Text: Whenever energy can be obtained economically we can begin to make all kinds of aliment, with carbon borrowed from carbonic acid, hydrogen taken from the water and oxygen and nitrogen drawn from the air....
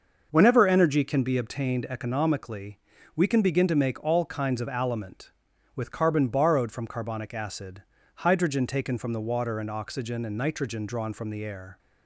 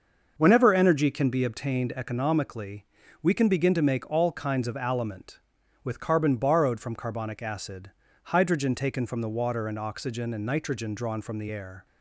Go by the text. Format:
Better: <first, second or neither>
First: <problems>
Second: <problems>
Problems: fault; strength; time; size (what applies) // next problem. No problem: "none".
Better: neither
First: starts louder than the rest; until 1.3 s; 6 dB // pauses between "economically" and "we"; slight; at 2.7 s; 0.34 s long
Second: starts louder than the rest; until 1.3 s; 6 dB // pauses between "economically" and "we"; slight; at 2.8 s; 0.34 s long